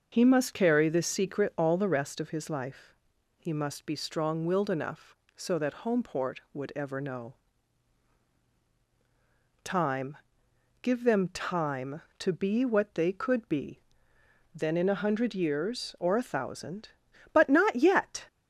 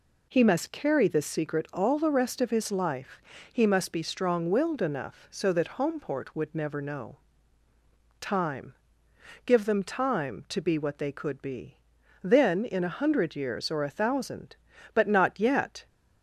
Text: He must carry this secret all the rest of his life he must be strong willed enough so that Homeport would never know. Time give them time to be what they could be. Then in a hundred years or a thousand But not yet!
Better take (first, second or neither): second